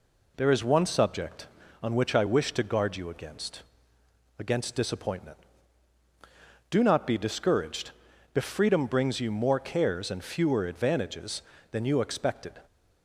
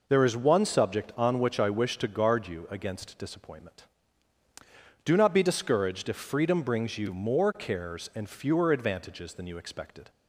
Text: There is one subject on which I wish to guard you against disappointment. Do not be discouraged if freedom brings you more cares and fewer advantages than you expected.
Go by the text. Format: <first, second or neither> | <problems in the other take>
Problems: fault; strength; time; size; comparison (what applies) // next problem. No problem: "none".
second | says "against" twice; at 4.3 s // pauses between "discouraged" and "if"; at 7.9 s; 0.42 s long